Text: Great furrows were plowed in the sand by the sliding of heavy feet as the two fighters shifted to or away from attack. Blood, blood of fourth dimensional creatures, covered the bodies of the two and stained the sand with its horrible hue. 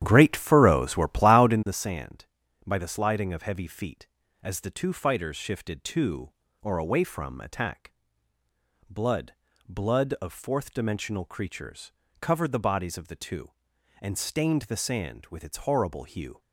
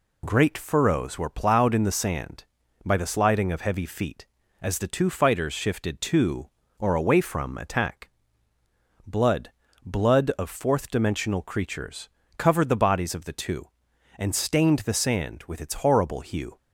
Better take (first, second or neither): second